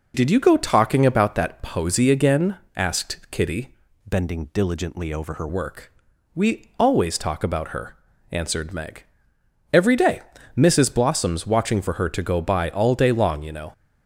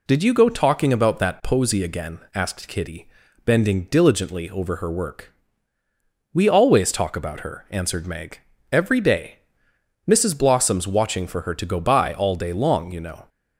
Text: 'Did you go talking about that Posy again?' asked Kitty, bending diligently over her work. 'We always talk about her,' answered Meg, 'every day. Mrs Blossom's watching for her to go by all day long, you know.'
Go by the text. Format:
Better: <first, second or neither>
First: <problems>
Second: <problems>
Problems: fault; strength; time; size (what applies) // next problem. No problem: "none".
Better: second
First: changes voice from "bending" to "her"; from 4.0 to 5.4 s; 1.4 s long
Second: none